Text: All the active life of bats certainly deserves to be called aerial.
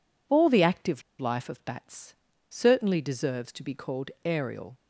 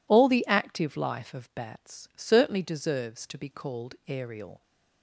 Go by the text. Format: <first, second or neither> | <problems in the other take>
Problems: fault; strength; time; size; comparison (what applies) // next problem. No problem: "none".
second | pauses between "active" and "life"; slight; at 1.0 s; 0.17 s long // pauses between "bats" and "certainly"; slight; at 2.1 s; 0.34 s long // pauses between "called" and "aerial"; slight; at 4.0 s; 0.16 s long